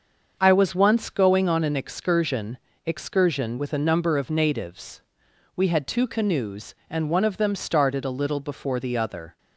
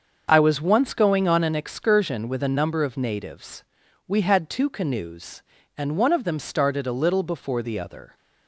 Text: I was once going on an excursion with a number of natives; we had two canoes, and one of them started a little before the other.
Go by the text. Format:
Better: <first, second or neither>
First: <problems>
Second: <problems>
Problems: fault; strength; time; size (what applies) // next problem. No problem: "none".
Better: second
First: starts louder than the rest; until 1.4 s; 7 dB // says "excursion" twice; at 2.8 s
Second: starts louder than the rest; until 1.3 s; 6.5 dB